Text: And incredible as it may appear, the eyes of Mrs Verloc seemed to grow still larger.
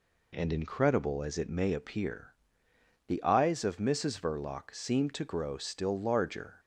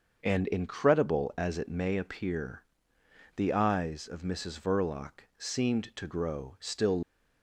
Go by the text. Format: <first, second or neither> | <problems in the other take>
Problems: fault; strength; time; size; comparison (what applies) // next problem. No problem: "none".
first | starts louder than the rest; until 1.2 s; 6.5 dB // pauses between "Verloc" and "seemed"; slight; at 5.2 s; 0.18 s long // stops before "larger"; at 7.0 s